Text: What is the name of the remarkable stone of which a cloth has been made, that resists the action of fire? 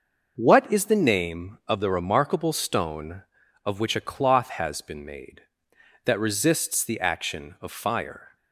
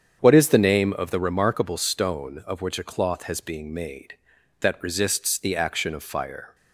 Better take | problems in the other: first | starts louder than the rest; strong; until 1.2 s; 8 dB // says "being" for "been"; at 3.3 s

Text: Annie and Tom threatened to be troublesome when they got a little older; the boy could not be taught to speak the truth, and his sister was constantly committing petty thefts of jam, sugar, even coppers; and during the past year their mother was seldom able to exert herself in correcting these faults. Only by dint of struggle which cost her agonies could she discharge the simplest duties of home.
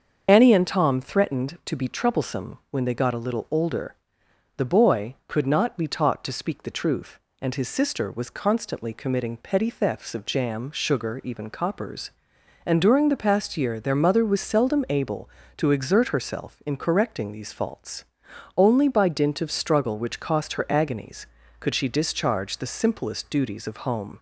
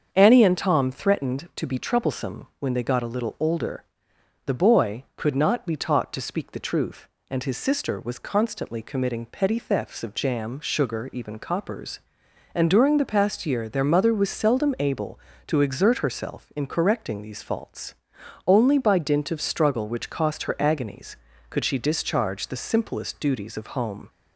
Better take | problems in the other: second | loses the start of "Annie"; at 0.2 s; 60 ms // starts louder than the rest; until 1.2 s; 7 dB; also in the second

